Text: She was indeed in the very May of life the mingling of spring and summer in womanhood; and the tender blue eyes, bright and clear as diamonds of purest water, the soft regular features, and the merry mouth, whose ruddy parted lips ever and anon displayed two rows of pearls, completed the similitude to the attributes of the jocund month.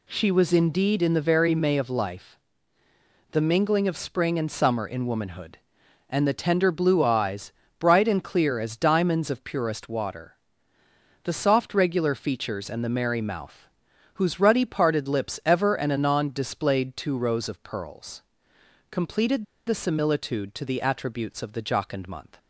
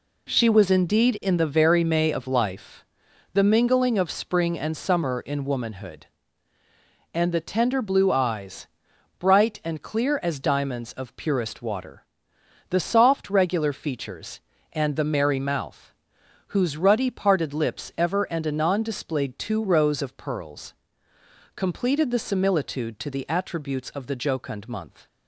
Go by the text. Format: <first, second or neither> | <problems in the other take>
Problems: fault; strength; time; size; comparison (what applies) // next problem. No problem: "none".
second | pauses between "life" and "the"; noticeable; at 2.3 s; 0.94 s long; noticeable in the second // pauses between "completed" and "the"; slight; at 19.4 s; 0.23 s long